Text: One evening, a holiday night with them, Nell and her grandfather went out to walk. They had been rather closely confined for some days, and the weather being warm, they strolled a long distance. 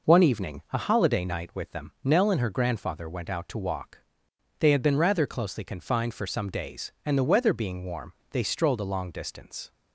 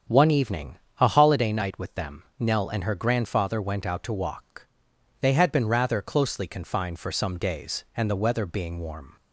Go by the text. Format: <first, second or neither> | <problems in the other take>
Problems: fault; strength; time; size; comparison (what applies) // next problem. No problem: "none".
first | starts louder than the rest; strong; until 1.3 s; 8 dB // stops before "they strolled a long distance"; at 9.1 s